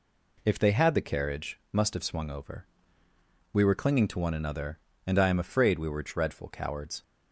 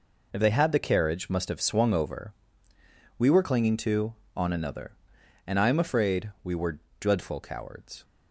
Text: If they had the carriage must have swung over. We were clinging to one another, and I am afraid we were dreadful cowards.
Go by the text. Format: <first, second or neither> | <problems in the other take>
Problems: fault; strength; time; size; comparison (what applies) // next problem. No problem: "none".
first | says "on" for "one"; at 4.3 s // pauses between "were" and "dreadful"; slight; at 6.7 s; 0.20 s long